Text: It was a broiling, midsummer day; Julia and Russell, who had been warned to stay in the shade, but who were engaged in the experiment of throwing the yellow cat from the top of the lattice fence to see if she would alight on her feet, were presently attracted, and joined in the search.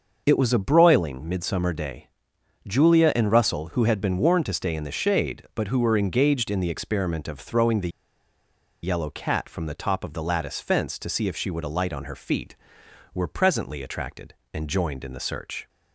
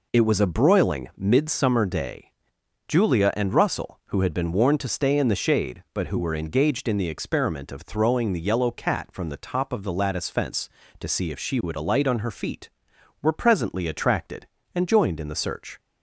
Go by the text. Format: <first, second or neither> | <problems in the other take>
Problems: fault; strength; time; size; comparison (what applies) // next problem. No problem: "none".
second | starts louder than the rest; noticeable; until 1.2 s; 6 dB // pauses between "the" and "yellow"; noticeable; at 7.9 s; 0.92 s long